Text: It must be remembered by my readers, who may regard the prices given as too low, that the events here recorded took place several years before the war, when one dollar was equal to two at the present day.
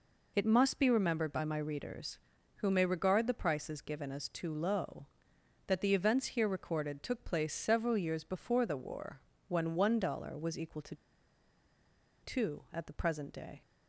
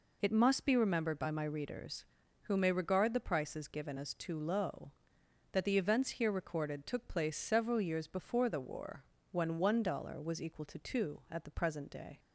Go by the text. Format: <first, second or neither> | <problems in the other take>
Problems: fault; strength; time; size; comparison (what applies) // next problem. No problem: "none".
second | pauses between "to" and "two"; strong; at 10.9 s; 1.2 s long